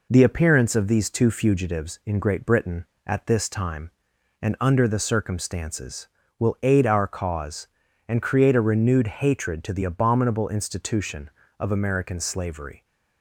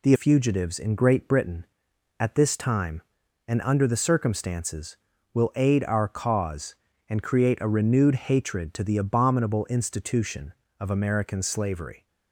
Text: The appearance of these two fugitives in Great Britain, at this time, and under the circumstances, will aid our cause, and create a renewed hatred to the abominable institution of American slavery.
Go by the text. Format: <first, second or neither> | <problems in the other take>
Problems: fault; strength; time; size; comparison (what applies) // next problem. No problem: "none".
first | skips "appearance of these two"; at 0.1 s